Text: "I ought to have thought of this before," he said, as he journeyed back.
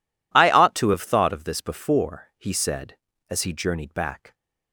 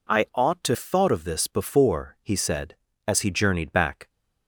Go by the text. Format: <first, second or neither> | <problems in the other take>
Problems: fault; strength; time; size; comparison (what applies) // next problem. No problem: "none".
first | skips "have"; at 0.7 s